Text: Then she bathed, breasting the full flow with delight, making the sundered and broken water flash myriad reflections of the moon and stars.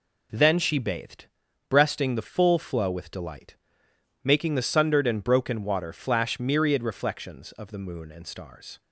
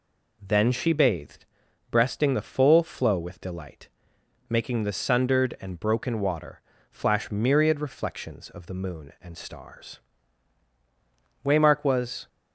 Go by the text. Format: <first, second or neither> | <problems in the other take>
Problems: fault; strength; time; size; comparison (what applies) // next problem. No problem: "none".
first | pauses between "water" and "flash"; slight; at 6.6 s; 0.30 s long // goes on to say "Waymark was"; noticeable; from 11.4 s on; 0.84 s long